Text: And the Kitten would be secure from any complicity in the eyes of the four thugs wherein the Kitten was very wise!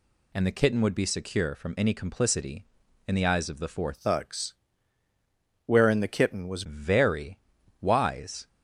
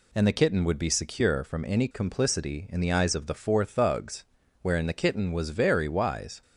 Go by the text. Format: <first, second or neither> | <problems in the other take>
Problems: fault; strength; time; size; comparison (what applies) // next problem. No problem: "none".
second | changes voice from "thugs" to "was"; from 3.9 to 6.6 s; 2.7 s long // pauses between "thugs" and "wherein"; at 4.5 s; 1.1 s long; also in the second // pauses between "very" and "wise"; at 7.3 s; 0.44 s long